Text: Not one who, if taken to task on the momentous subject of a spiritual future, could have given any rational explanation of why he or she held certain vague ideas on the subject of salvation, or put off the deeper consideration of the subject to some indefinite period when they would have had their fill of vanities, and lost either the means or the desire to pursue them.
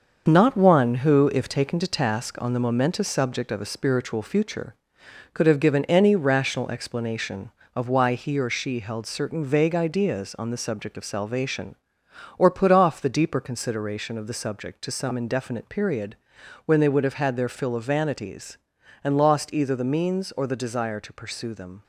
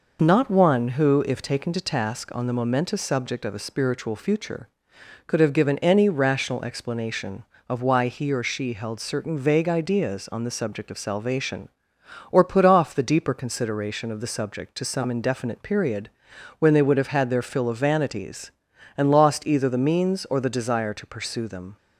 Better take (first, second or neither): second